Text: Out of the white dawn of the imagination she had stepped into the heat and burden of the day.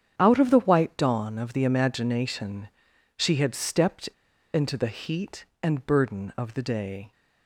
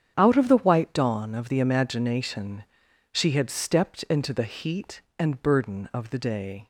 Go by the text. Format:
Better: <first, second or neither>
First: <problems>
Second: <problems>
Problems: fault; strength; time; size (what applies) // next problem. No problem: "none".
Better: second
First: starts louder than the rest; strong; until 1.1 s; 8.5 dB // pauses between "imagination" and "she"; noticeable; at 2.6 s; 0.48 s long // pauses between "stepped" and "into"; at 4.0 s; 0.45 s long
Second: starts louder than the rest; strong; until 1.1 s; 8.5 dB // pauses between "imagination" and "she"; noticeable; at 2.6 s; 0.48 s long